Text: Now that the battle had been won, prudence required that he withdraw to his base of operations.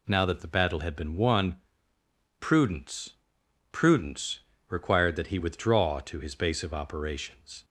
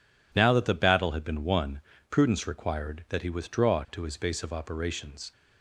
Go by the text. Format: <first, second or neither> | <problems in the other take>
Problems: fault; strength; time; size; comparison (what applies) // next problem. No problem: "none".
second | says "prudence" twice; at 3.7 s